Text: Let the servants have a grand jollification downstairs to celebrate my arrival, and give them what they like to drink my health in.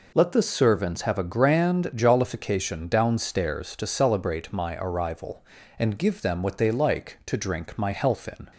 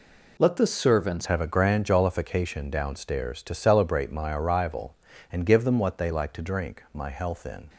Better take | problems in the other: first | changes voice at "have"; from 1.2 s on; 6.4 s long

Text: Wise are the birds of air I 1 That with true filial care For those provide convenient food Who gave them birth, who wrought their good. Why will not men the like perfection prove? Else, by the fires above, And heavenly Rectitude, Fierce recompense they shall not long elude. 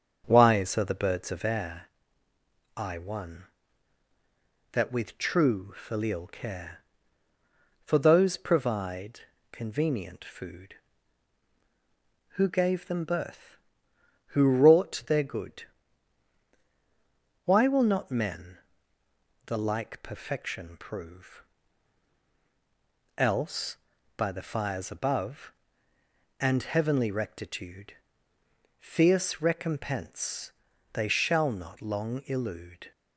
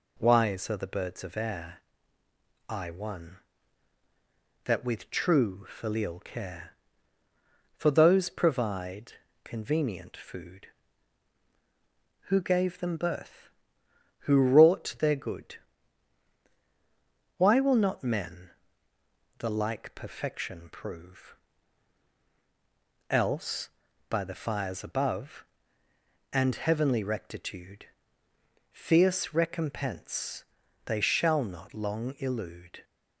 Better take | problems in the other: second | starts louder than the rest; strong; until 1.8 s; 7 dB // pauses between "air" and "I"; noticeable; at 1.8 s; 0.88 s long; noticeable in the second // pauses between "provide" and "convenient"; slight; at 9.1 s; 0.32 s long; slight in the second // pauses between "men" and "the"; noticeable; at 18.5 s; 0.88 s long; noticeable in the second // pauses between "recompense" and "they"; at 30.5 s; 0.42 s long; also in the second

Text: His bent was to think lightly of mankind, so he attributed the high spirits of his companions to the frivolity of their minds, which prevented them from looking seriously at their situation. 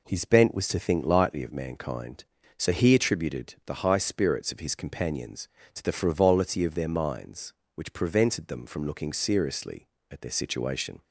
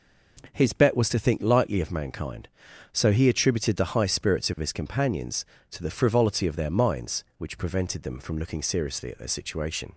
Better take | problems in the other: first | says "bet" for "bent"; at 0.7 s

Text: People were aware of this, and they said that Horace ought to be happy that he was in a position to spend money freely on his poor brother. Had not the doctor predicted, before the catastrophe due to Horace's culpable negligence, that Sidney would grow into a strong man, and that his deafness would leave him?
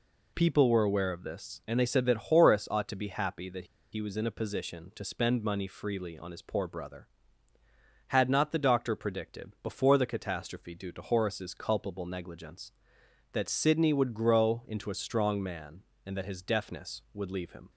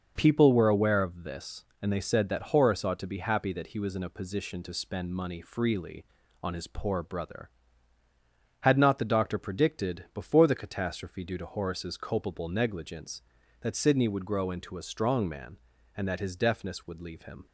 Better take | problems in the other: second | pauses between "that" and "he"; slight; at 3.6 s; 0.27 s long

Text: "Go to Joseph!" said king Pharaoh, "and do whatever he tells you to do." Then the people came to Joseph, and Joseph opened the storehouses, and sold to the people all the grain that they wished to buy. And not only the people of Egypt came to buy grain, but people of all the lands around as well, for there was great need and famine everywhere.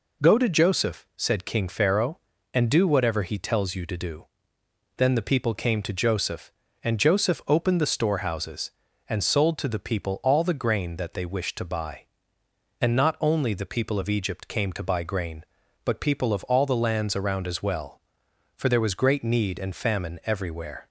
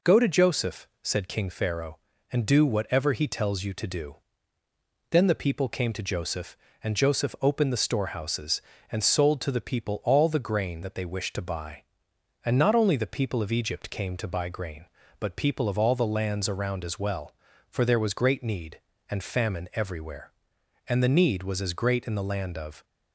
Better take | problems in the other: first | goes on to say "And the need was as great in the land of"; strong; from 20.8 s on; 1.9 s long

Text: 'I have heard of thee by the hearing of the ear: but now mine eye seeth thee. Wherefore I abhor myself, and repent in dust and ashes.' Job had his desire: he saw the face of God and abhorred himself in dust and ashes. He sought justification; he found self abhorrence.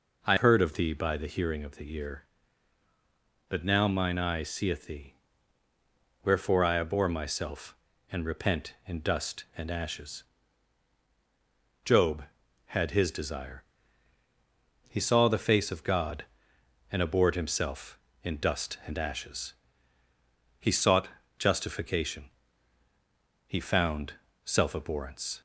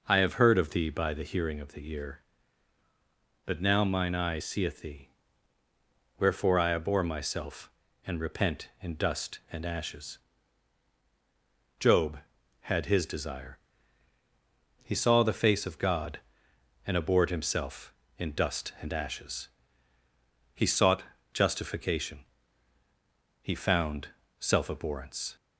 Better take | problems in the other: second | skips "have"; at 0.3 s // pauses between "sought" and "justification"; slight; at 21.0 s; 0.28 s long; slight in the second // pauses between "found" and "self"; slight; at 24.1 s; 0.32 s long; slight in the second

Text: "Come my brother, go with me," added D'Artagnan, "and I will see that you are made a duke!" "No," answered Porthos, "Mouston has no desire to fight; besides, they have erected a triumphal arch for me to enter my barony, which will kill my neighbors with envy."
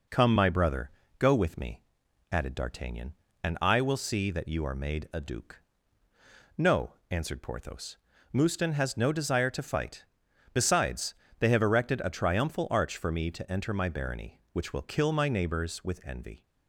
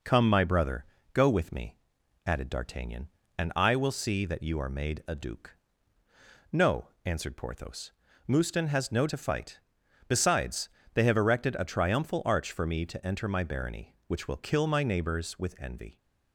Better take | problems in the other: first | skips "desire"; at 9.0 s

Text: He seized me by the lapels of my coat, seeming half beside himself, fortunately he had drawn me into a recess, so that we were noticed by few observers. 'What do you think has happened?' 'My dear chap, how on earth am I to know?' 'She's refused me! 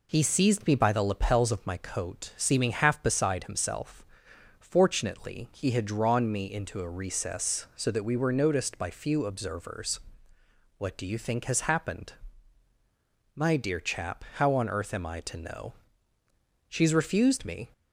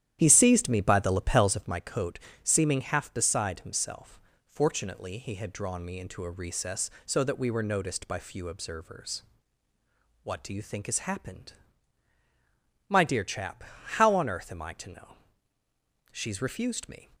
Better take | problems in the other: first | starts louder than the rest; strong; until 1.8 s; 11.5 dB

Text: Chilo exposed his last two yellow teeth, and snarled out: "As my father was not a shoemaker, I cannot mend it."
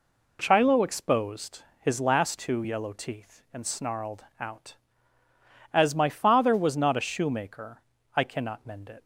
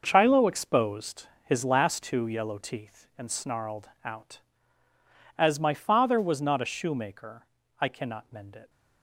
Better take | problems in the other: first | gets quieter; strong; throughout; 10.5 dB // pauses between "exposed" and "his"; slight; at 1.2 s; 0.16 s long; slight in the first // pauses between "snarled" and "out"; slight; at 3.8 s; 0.16 s long; slight in the first

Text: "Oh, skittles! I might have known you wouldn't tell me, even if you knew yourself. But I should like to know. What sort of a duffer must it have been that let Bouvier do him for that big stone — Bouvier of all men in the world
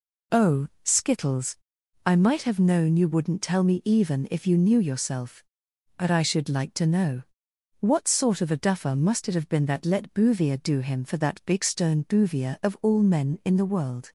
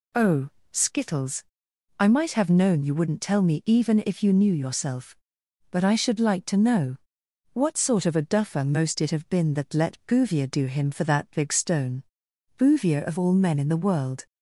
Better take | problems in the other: first | says "most" for "must"; at 8.6 s

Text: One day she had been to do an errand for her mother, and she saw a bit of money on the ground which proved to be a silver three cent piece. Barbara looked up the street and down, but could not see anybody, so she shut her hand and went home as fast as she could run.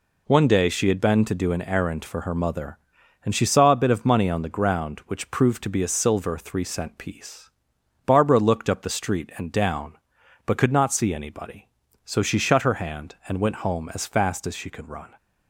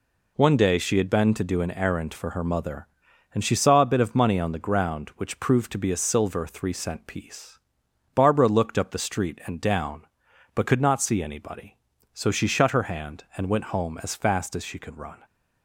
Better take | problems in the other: neither | none

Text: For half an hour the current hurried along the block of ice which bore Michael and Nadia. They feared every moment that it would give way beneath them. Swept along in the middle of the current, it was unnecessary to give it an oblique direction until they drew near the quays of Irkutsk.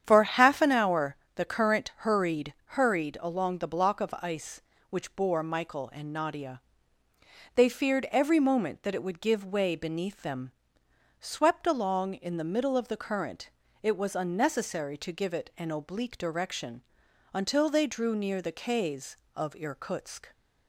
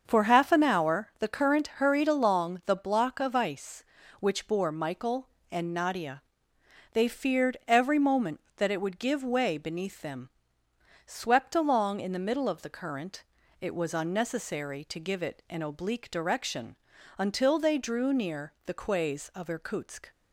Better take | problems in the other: second | starts louder than the rest; strong; until 1.0 s; 9 dB; also in the second // pauses between "hour" and "the"; slight; at 1.1 s; 0.18 s long // says "hurried" twice; at 2.6 s // pauses between "direction" and "until"; noticeable; at 16.8 s; 0.50 s long; also in the second

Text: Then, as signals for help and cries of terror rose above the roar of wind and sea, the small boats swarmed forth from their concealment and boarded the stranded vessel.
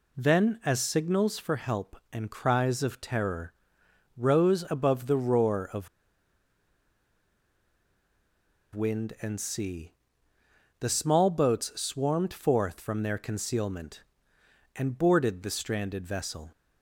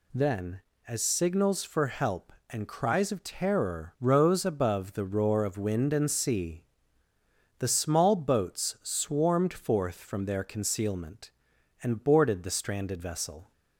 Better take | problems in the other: second | pauses between "terror" and "rose"; noticeable; at 3.5 s; 0.64 s long // pauses between "of" and "wind"; strong; at 5.8 s; 2.8 s long

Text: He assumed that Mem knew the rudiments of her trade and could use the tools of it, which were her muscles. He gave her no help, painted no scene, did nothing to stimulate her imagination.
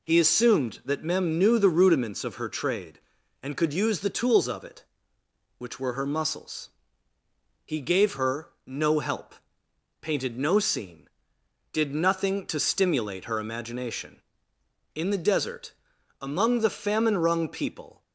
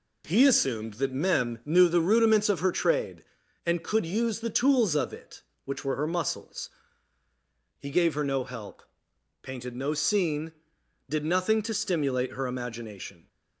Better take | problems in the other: second | pauses between "her" and "no"; slight; at 8.4 s; 0.18 s long // goes on to say "In the desert among the famine wrung people"; strong; from 14.9 s on; 3.0 s long

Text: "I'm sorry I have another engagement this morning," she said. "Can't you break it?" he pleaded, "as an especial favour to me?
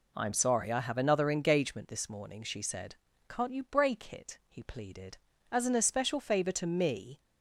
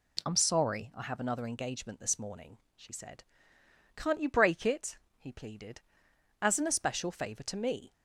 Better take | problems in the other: neither | none

